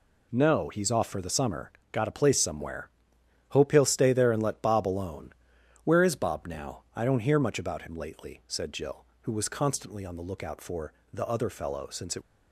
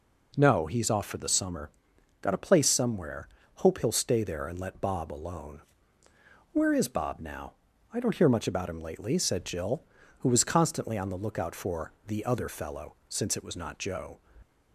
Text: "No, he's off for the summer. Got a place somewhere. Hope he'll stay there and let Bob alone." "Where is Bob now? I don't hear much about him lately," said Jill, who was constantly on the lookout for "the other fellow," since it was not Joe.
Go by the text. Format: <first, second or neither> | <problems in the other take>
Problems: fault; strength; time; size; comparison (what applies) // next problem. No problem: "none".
second | pauses between "for" and "the"; slight; at 10.9 s; 0.18 s long; slight in the second // stops before "was not Joe"; at 12.2 s